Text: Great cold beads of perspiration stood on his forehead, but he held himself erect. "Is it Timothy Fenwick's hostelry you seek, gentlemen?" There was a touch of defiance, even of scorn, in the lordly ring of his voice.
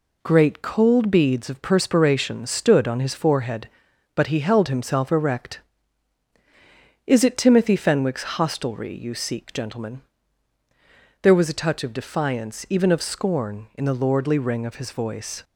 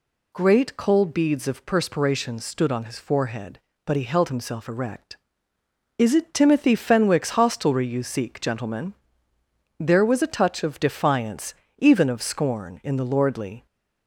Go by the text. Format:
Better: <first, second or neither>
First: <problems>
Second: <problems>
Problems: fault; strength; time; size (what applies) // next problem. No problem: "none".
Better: first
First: none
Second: stops before "ring of his voice"; at 13.6 s